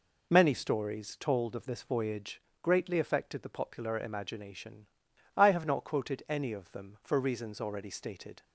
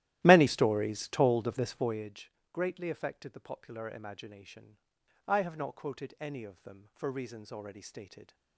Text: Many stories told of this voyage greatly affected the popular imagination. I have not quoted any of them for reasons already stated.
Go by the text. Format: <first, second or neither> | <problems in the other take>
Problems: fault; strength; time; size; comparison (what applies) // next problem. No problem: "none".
first | starts louder than the rest; strong; until 2.1 s; 14 dB // pauses between "voyage" and "greatly"; slight; at 2.3 s; 0.22 s long; slight in the first